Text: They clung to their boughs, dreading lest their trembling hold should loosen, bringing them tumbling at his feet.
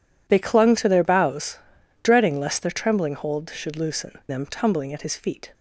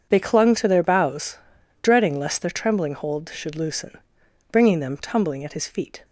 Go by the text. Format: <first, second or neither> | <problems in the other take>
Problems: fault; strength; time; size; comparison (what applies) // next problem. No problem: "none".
second | skips "bringing"; at 4.2 s